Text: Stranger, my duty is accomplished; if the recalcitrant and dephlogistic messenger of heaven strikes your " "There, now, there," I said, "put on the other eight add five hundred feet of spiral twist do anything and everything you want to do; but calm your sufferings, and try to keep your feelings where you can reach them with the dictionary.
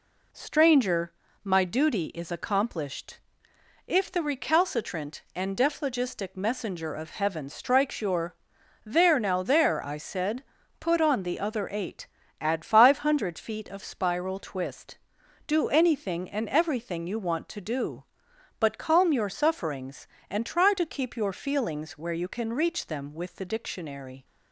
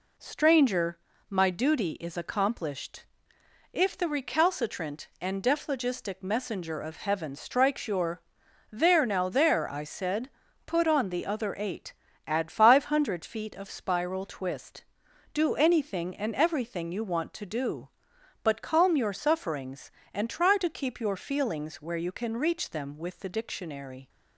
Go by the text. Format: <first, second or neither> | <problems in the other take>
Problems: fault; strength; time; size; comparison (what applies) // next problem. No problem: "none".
neither | pauses between "eight" and "add"; slight; the same in both